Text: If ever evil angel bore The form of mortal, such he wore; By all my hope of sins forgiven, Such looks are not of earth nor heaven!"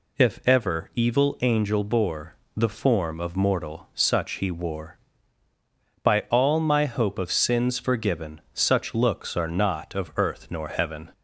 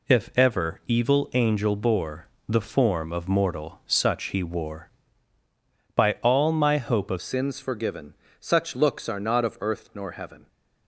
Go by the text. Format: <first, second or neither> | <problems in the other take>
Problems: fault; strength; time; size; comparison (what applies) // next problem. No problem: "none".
first | pauses between "bore" and "The"; slight; at 2.2 s; 0.20 s long; slight in the first // changes voice at "sins"; from 7.2 s on; 3.2 s long